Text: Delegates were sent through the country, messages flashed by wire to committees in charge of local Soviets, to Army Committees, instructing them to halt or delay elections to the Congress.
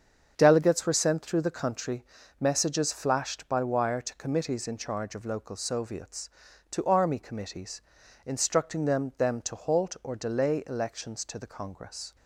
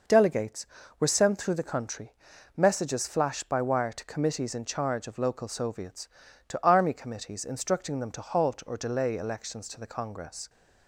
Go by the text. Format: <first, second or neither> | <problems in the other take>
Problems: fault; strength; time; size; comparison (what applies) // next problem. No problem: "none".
second | starts louder than the rest; strong; until 1.3 s; 7 dB // says "them" twice; at 9.1 s